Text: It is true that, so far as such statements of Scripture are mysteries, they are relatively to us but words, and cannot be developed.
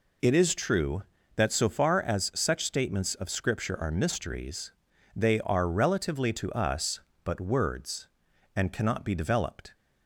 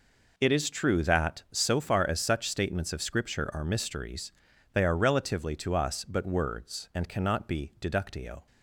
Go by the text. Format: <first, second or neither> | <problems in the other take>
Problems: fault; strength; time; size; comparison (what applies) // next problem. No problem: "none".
first | says "deductio" for "developed"; at 7.7 s